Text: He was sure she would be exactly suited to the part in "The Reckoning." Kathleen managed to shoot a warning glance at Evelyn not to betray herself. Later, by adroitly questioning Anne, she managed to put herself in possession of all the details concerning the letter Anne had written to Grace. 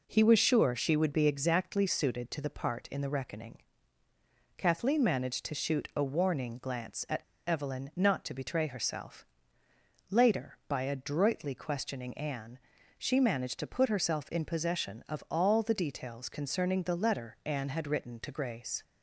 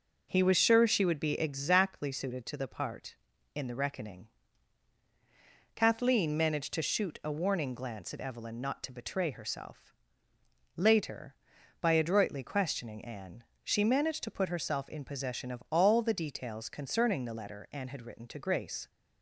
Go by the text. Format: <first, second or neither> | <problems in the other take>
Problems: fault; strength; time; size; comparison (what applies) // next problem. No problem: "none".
second | pauses between "at" and "Evelyn"; slight; at 7.2 s; 0.23 s long